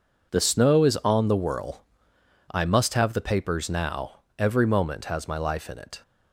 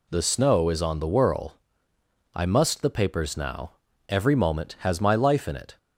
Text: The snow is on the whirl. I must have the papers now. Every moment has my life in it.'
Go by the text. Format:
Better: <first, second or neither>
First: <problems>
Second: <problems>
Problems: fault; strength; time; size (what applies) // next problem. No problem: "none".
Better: first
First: none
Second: skips "have"; at 2.8 s